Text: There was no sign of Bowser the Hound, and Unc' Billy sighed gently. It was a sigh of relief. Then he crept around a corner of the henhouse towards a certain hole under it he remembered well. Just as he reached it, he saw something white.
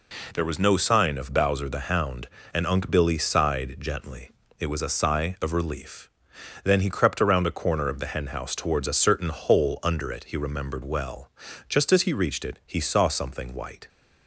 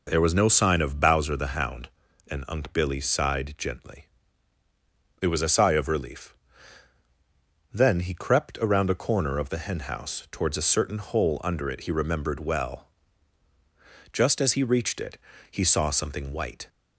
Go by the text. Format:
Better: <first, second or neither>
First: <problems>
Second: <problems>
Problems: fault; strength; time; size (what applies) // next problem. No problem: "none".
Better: neither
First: none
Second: none